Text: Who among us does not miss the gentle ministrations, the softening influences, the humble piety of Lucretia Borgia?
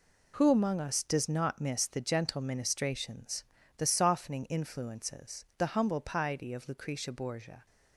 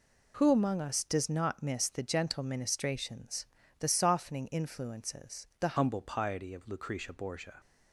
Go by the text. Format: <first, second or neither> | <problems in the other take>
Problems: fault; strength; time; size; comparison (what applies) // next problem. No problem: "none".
first | changes voice at "humble"; from 5.7 s on; 1.9 s long